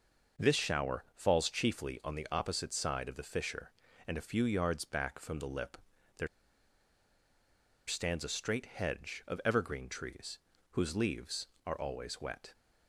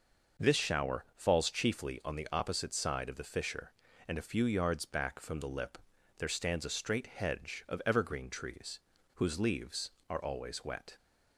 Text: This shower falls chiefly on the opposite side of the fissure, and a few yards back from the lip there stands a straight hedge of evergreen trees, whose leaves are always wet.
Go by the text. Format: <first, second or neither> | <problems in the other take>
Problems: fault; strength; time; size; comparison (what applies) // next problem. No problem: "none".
second | pauses between "lip" and "there"; at 5.7 s; 0.40 s long; also in the second // pauses between "there" and "stands"; strong; at 6.2 s; 1.6 s long